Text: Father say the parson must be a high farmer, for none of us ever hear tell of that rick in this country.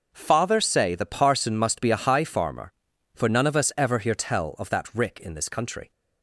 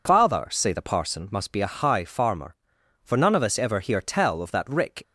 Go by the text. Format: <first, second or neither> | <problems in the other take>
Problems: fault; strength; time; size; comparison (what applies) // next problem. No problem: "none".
first | stops before "in this country"; at 5.0 s